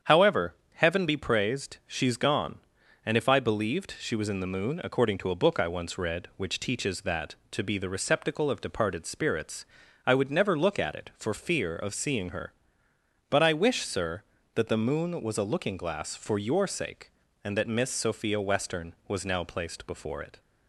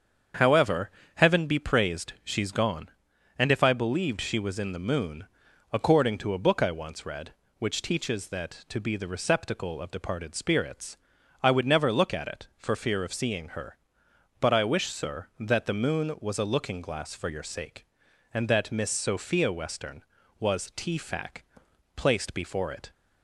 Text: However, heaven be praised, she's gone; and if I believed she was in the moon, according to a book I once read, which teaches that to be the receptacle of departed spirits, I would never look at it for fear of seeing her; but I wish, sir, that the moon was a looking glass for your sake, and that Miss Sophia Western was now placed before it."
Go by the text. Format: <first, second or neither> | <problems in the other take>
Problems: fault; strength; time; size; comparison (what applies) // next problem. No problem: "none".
first | starts louder than the rest; strong; until 1.6 s; 7.5 dB; strong in the first // says "tfac" for "now"; at 20.7 s